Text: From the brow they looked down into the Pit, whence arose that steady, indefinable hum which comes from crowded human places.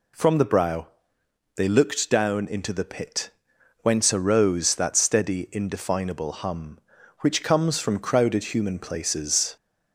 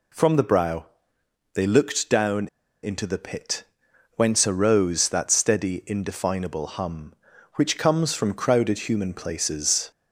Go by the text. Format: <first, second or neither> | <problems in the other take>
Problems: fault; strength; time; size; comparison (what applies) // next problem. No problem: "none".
first | pauses between "brow" and "they"; noticeable; at 0.8 s; 0.70 s long; noticeable in the first // pauses between "down" and "into"; at 2.4 s; 0.36 s long